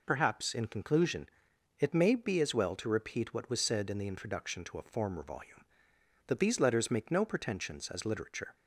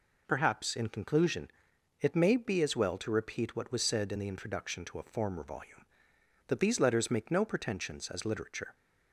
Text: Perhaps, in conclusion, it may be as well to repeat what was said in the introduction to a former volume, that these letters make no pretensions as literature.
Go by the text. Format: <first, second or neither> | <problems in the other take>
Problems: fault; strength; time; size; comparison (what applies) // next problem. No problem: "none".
neither | none